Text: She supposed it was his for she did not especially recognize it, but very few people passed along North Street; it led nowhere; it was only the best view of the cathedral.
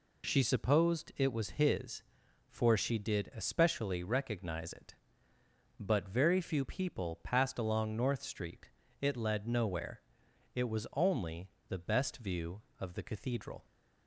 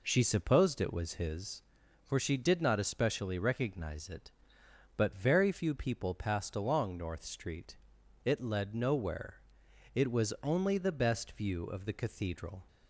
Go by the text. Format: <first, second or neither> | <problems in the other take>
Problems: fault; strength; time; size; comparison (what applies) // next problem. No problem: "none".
second | skips "not"; at 3.3 s // pauses between "only" and "the"; slight; at 11.4 s; 0.20 s long